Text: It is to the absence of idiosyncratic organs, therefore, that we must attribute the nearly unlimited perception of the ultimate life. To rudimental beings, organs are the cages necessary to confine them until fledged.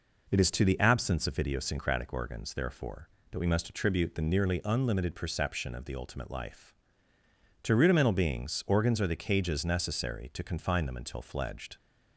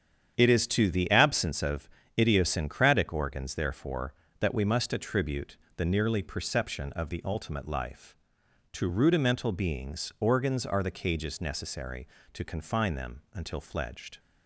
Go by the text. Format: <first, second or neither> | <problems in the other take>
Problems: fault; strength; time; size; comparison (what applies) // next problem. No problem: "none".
first | starts louder than the rest; strong; until 1.3 s; 8.5 dB // pauses between "of" and "idiosyncratic"; slight; at 1.8 s; 0.32 s long // pauses between "attribute" and "the"; slight; at 5.5 s; 0.21 s long // skips "unlimited"; at 6.2 s